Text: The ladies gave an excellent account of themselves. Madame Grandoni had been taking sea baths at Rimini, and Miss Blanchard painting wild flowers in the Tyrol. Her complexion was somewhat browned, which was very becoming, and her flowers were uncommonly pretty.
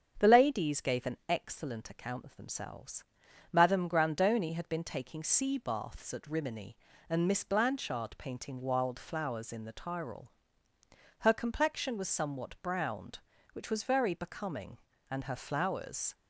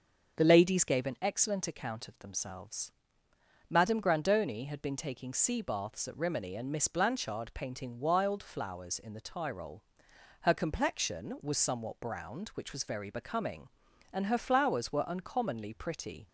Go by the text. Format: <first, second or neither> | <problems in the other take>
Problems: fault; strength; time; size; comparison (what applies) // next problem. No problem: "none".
second | starts louder than the rest; strong; until 1.1 s; 7.5 dB; also in the second // stops before "were uncommonly pretty"; at 16.1 s